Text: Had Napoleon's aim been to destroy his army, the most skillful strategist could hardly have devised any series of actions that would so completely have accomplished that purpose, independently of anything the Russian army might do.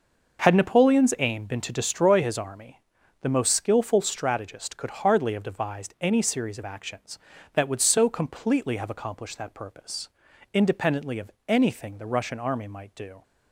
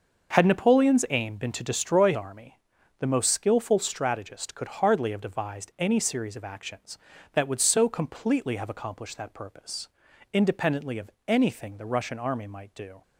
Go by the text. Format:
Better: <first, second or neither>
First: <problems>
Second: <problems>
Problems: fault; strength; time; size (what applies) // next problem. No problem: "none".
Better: first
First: pauses between "of" and "anything"; slight; at 11.3 s; 0.16 s long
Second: starts louder than the rest; until 1.3 s; 6 dB // skips "his"; at 2.1 s // pauses between "of" and "anything"; slight; at 11.1 s; 0.16 s long